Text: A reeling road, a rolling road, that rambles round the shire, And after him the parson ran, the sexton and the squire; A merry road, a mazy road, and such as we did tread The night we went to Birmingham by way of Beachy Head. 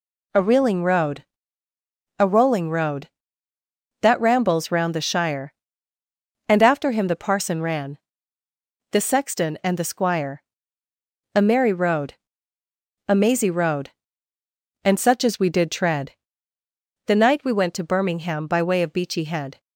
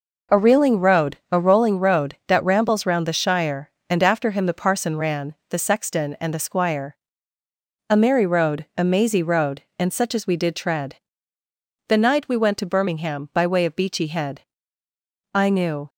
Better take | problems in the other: first | pauses between "tread" and "The"; noticeable; at 10.9 s; 0.90 s long; noticeable in the first // goes on to say "I knew"; from 15.3 s on; 0.56 s long

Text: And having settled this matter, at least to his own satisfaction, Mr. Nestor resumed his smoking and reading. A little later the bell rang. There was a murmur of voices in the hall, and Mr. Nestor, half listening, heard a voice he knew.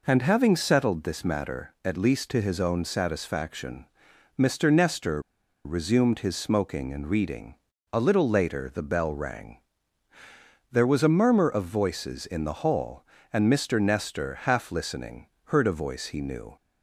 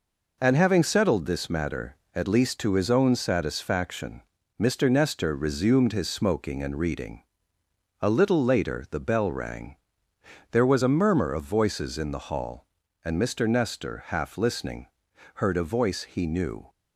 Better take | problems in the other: second | pauses between "Nestor" and "resumed"; at 5.2 s; 0.43 s long

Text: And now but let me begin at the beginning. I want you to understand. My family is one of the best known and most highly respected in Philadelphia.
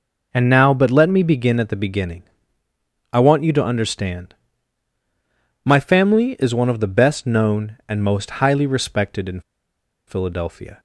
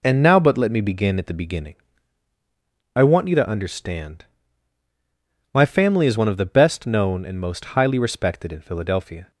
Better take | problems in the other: second | pauses between "in" and "Philadelphia"; noticeable; at 9.4 s; 0.66 s long

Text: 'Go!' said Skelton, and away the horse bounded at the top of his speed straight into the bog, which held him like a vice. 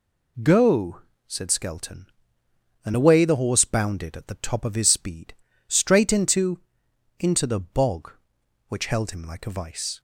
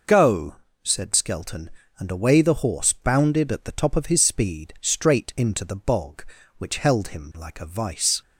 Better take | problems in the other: second | pauses between "speed" and "straight"; slight; at 5.3 s; 0.34 s long // says "into" twice; at 7.1 s

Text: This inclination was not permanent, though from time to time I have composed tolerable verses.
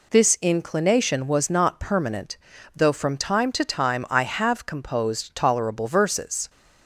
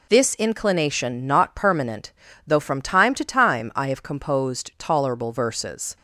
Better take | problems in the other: first | skips "was"; at 1.2 s

